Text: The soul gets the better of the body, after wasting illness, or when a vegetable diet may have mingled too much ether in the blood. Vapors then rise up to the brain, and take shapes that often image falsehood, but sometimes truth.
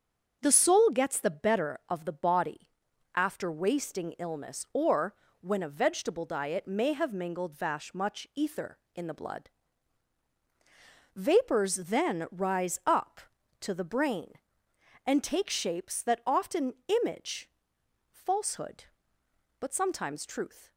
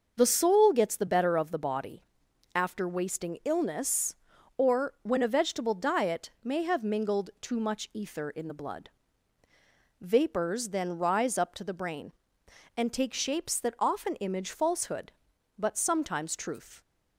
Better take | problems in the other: second | starts louder than the rest; strong; until 1.4 s; 7 dB; noticeable in the second // pauses between "or" and "when"; slight; at 5.1 s; 0.26 s long // says "vash" for "too"; at 7.5 s // pauses between "often" and "image"; slight; at 16.7 s; 0.30 s long // pauses between "image" and "falsehood"; noticeable; at 17.4 s; 0.62 s long

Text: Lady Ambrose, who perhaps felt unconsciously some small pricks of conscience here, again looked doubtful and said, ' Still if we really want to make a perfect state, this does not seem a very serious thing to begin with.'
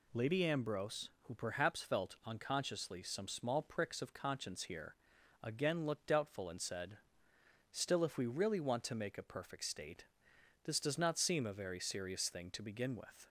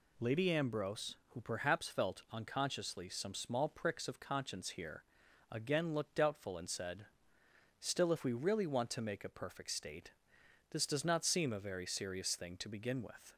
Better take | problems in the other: neither | none

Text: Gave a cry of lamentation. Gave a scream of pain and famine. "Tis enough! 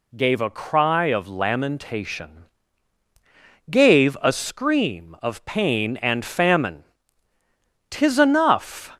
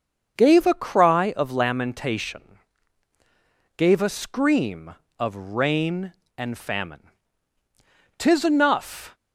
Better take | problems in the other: first | starts louder than the rest; until 1.3 s; 6.5 dB // says "rain" for "pain"; at 5.3 s

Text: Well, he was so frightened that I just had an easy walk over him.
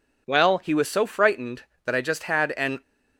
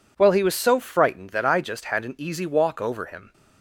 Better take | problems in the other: second | stops before "easy walk over him"; at 2.8 s

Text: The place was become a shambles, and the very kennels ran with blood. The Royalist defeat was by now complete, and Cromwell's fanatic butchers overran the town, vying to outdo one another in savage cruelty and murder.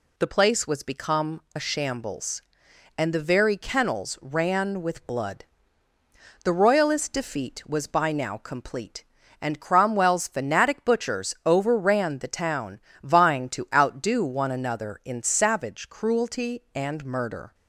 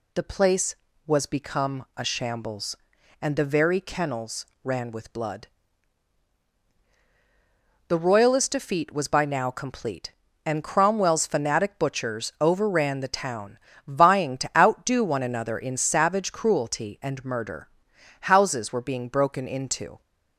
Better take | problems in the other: first | pauses between "kennels" and "ran"; slight; at 4.4 s; 0.20 s long // goes on to say "Houses were being broken into"; strong; from 18.2 s on; 1.7 s long

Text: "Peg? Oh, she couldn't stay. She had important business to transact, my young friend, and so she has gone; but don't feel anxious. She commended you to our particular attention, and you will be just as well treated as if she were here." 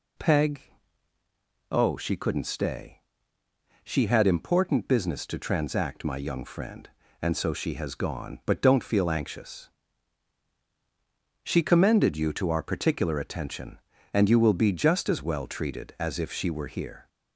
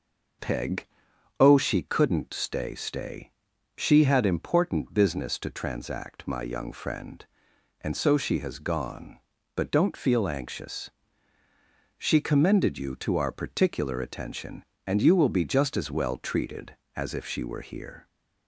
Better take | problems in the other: first | says "stay" twice; at 2.7 s

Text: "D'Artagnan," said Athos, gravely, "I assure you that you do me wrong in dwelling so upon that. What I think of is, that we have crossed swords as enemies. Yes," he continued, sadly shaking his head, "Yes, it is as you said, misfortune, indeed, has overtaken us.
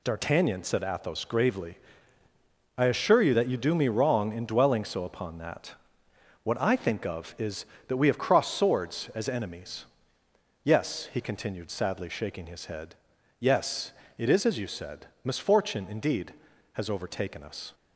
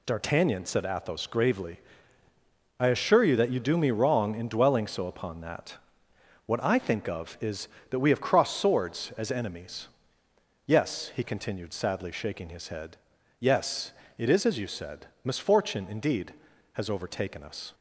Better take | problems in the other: neither | none

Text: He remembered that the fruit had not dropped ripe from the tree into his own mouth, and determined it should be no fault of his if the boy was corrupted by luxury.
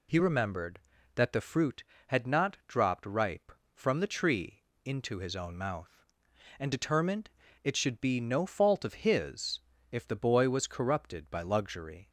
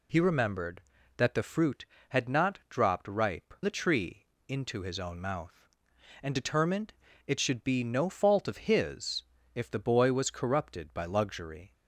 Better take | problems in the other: first | skips "from"; at 3.5 s // pauses between "tree" and "into"; slight; at 4.2 s; 0.20 s long; slight in the first // pauses between "determined" and "it"; slight; at 6.9 s; 0.34 s long; slight in the first // pauses between "his" and "if"; slight; at 9.2 s; 0.32 s long; slight in the first

